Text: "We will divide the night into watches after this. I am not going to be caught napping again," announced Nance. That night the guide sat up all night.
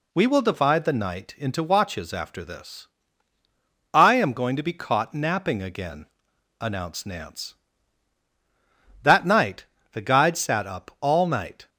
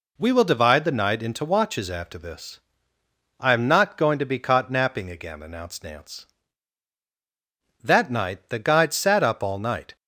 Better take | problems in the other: second | skips "not"; at 4.3 s // pauses between "night" and "the"; slight; at 9.6 s; 0.26 s long

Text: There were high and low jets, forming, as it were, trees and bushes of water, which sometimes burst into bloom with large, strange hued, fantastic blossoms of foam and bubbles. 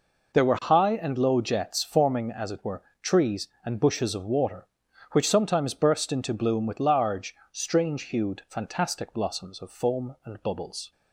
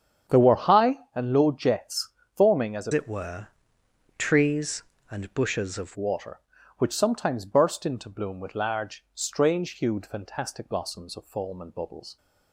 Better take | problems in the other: first | starts louder than the rest; strong; until 1.4 s; 8.5 dB // changes voice from "it" to "of"; from 2.9 to 5.9 s; 3.0 s long

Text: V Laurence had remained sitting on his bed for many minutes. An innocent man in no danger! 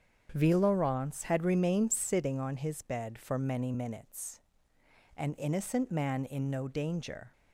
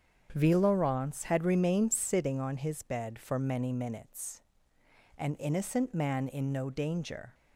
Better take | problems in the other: neither | starts louder than the rest; strong; the same in both

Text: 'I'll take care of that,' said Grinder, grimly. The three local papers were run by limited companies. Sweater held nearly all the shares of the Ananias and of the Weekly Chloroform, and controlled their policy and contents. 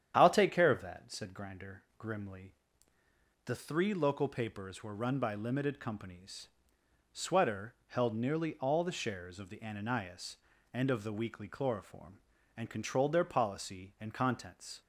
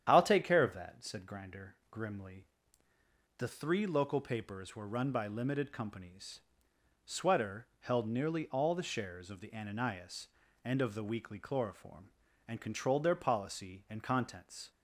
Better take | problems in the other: neither | starts louder than the rest; strong; the same in both

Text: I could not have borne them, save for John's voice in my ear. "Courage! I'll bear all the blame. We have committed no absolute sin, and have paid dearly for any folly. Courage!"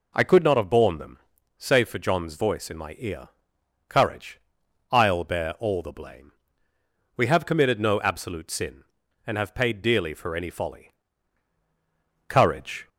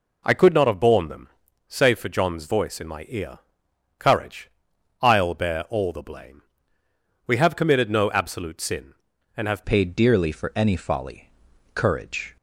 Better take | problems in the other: first | changes voice at "paid"; from 9.6 s on; 2.7 s long

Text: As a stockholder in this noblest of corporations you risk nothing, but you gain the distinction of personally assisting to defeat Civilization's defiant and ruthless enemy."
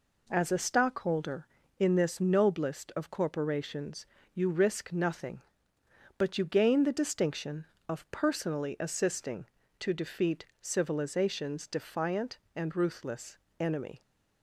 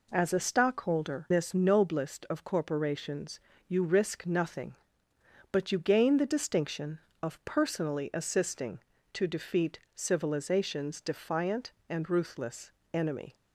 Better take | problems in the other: first | skips "in"; at 1.2 s // pauses between "corporations" and "you"; slight; at 3.4 s; 0.26 s long; slight in the first // pauses between "defeat" and "Civilization's"; slight; at 9.8 s; 0.16 s long; slight in the first // pauses between "ruthless" and "enemy"; slight; at 12.7 s; 0.22 s long; slight in the first

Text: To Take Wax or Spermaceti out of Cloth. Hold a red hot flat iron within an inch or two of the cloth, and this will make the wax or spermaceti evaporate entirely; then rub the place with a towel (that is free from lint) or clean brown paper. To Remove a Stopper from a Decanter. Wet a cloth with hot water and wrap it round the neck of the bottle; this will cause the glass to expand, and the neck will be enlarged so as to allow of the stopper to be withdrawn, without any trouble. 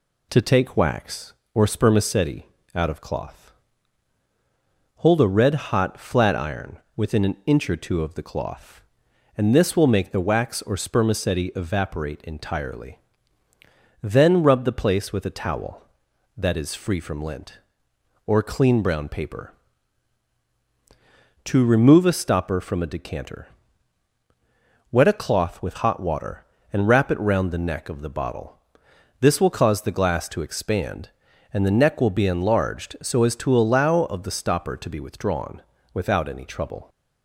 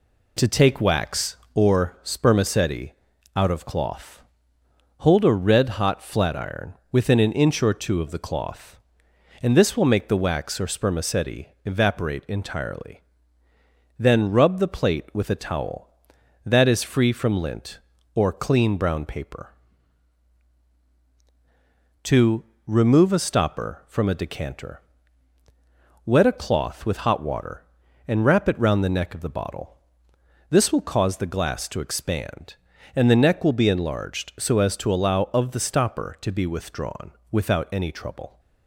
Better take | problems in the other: first | pauses between "Spermaceti" and "out"; at 2.9 s; 0.42 s long; slight in the first // pauses between "iron" and "within"; slight; at 6.7 s; 0.16 s long; slight in the first // pauses between "spermaceti" and "evaporate"; slight; at 11.4 s; 0.18 s long // says "plate" for "place"; at 14.6 s // pauses between "To" and "Remove"; slight; at 22.4 s; 0.24 s long

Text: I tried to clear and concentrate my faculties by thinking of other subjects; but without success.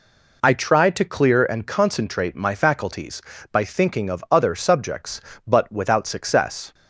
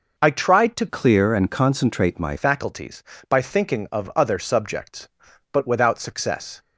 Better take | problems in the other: first | changes voice from "clear" to "my"; from 0.8 to 2.3 s; 1.5 s long

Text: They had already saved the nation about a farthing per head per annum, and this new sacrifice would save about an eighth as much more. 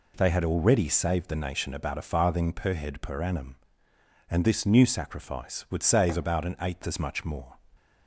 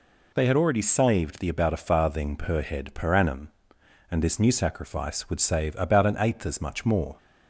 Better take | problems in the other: first | skips "nation"; at 1.4 s

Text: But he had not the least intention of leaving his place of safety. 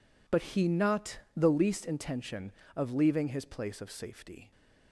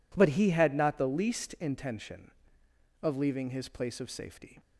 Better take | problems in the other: second | skips "had"; at 0.6 s // pauses between "not" and "the"; slight; at 1.1 s; 0.16 s long

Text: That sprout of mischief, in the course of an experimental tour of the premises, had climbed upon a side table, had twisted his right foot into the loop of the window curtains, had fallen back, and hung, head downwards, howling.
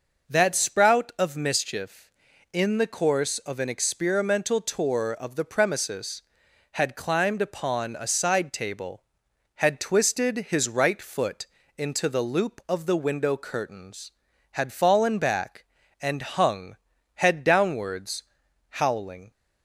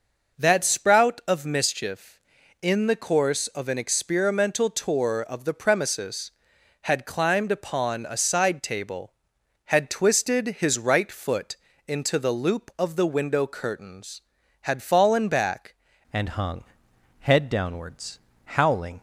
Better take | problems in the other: first | pauses between "foot" and "into"; slight; at 11.5 s; 0.32 s long; slight in the first // changes voice at "and"; from 16.1 s on; 2.9 s long

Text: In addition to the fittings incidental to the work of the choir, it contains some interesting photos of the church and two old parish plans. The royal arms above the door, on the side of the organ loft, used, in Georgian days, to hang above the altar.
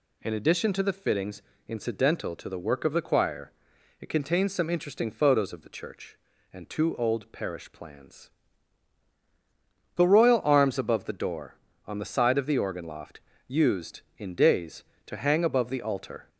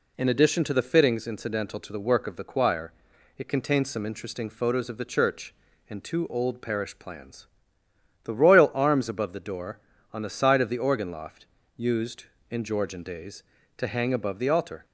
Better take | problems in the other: second | pauses between "fittings" and "incidental"; slight; at 1.4 s; 0.26 s long // skips "Georgian"; at 14.3 s

